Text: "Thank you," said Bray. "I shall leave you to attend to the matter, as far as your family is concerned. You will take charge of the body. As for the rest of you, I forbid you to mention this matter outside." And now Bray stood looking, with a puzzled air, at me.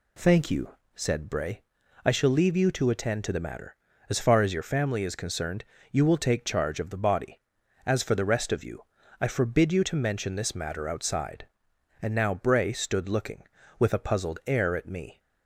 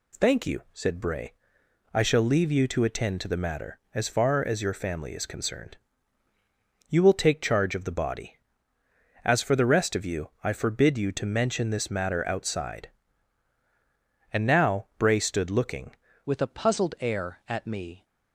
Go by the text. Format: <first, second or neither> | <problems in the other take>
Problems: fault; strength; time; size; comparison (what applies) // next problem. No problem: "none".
first | changes voice at "with"; from 16.2 s on; 1.8 s long